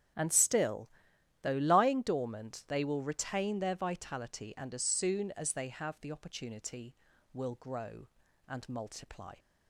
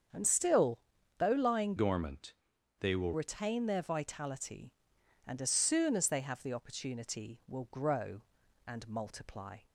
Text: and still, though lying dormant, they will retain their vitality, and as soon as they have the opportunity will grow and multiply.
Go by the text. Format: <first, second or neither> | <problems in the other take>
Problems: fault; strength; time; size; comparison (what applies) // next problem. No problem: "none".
first | starts louder than the rest; strong; until 1.5 s; 7.5 dB; strong in the first // changes voice from "dormant" to "will"; from 1.7 to 3.1 s; 1.4 s long